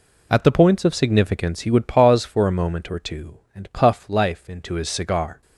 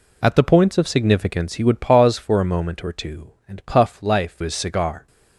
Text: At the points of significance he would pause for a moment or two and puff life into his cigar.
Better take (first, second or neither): first